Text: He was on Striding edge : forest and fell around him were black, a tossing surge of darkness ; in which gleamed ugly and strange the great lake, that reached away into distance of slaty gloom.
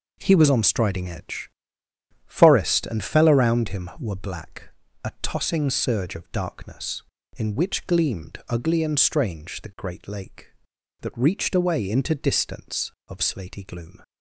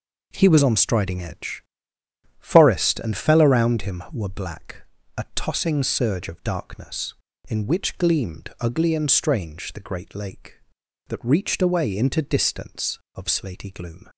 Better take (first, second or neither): neither